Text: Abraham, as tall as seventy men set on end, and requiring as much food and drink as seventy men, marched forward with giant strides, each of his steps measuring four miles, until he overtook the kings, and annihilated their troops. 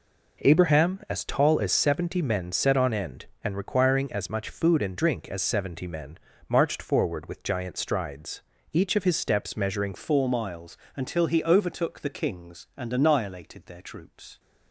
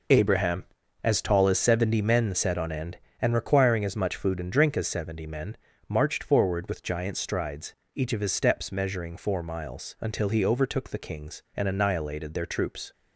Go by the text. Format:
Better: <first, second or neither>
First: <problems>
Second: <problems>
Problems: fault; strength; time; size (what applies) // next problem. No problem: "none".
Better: second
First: changes voice at "four"; from 9.9 s on; 4.4 s long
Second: none